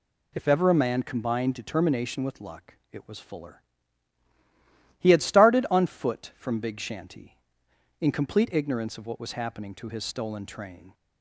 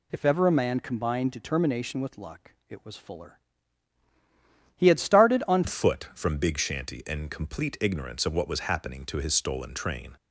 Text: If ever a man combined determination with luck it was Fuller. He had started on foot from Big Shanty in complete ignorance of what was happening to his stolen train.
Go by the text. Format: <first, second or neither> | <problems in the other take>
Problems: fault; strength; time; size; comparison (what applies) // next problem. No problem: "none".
first | pauses between "luck" and "it"; slight; at 2.5 s; 0.16 s long; slight in the first // changes voice at "foot"; from 5.6 s on; 4.5 s long